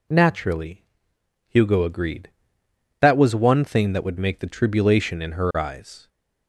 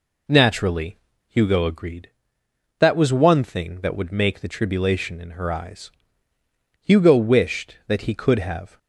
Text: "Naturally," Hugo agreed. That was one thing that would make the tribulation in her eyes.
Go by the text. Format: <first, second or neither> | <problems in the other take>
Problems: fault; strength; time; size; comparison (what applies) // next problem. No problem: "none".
first | goes on to say "Hugo wished that he could have"; strong; from 6.8 s on; 1.9 s long